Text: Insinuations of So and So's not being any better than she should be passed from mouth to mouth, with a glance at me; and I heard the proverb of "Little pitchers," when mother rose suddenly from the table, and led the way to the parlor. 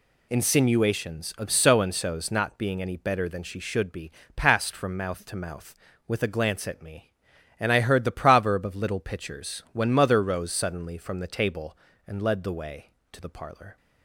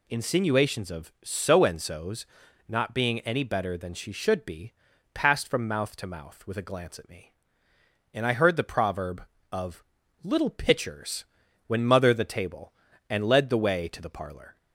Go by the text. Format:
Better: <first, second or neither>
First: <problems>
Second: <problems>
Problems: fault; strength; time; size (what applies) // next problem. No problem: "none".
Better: first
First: pauses between "be" and "passed"; slight; at 4.1 s; 0.26 s long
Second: pauses between "So's" and "not"; at 2.2 s; 0.44 s long // pauses between "be" and "passed"; at 4.7 s; 0.40 s long // pauses between "of" and "Little"; at 9.8 s; 0.40 s long // skips "rose suddenly from"; at 12.1 s